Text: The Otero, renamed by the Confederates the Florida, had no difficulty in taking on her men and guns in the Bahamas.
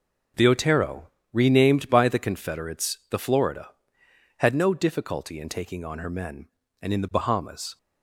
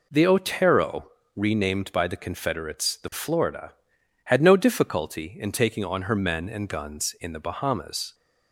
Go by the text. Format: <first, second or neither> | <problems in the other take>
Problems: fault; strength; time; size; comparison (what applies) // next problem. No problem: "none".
second | skips "guns"; at 6.9 s